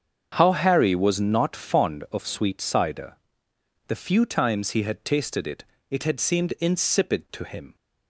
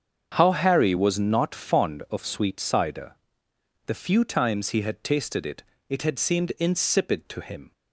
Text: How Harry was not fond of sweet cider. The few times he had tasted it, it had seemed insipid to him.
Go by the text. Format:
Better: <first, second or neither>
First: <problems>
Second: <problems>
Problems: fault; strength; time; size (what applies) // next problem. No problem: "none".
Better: neither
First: starts louder than the rest; strong; until 1.3 s; 7 dB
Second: starts louder than the rest; strong; until 1.3 s; 7.5 dB